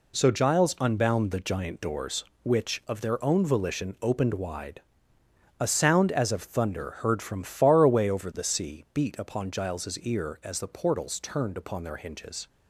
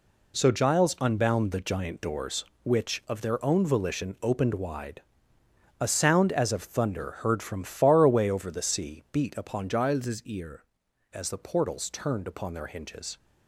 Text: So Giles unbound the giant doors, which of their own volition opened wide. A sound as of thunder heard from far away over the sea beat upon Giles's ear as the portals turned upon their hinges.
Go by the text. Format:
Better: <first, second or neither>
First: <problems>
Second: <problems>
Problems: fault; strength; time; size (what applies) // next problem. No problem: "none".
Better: first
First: none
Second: changes voice from "Giles's" to "ear"; from 9.6 to 10.6 s; 1.0 s long